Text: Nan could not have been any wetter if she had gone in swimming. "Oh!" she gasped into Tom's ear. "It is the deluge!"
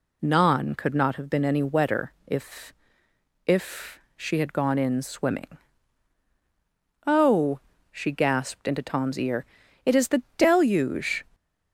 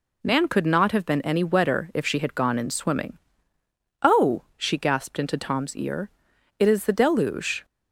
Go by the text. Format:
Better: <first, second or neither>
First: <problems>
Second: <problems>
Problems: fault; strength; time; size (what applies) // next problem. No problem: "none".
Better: second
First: says "if" twice; at 3.4 s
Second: none